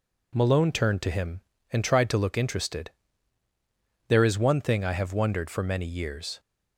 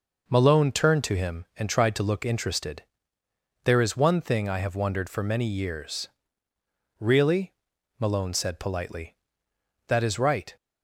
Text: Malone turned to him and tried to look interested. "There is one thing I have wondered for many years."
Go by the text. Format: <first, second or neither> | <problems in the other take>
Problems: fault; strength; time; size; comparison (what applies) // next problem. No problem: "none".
first | goes on to say "Really Malone said politely That is right"; strong; from 6.9 s on; 3.5 s long